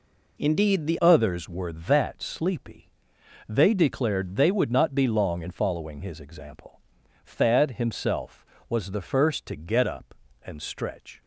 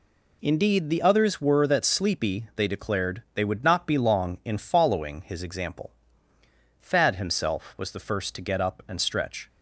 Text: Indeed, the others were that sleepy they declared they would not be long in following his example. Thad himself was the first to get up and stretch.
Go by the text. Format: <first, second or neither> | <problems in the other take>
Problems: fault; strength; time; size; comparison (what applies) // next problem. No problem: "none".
second | changes voice at "others"; from 1.0 s on; 10.2 s long // pauses between "sleepy" and "they"; noticeable; at 2.8 s; 0.66 s long